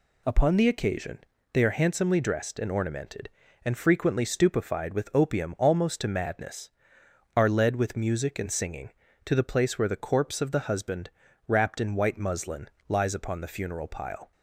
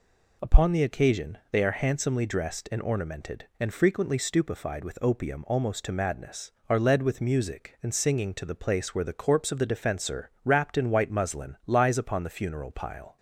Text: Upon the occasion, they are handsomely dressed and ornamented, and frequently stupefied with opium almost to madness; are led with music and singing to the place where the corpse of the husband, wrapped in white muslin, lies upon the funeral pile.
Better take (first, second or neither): first